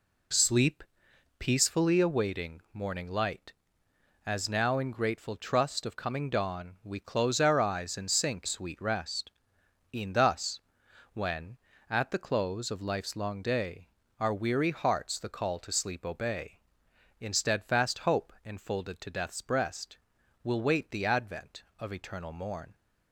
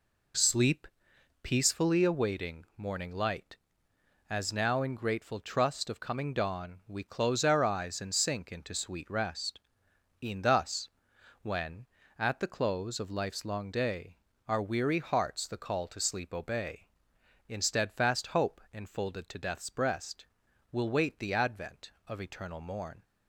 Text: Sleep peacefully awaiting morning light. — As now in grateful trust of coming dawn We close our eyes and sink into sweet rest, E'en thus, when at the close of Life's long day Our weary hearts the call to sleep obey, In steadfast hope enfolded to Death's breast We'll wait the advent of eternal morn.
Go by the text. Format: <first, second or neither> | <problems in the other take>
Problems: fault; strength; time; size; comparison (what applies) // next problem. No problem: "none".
second | pauses between "Sleep" and "peacefully"; noticeable; at 0.8 s; 0.58 s long; noticeable in the second // skips "into"; at 8.4 s // pauses between "day" and "Our"; slight; at 13.8 s; 0.32 s long; slight in the second // pauses between "breast" and "We'll"; noticeable; at 19.9 s; 0.48 s long; noticeable in the second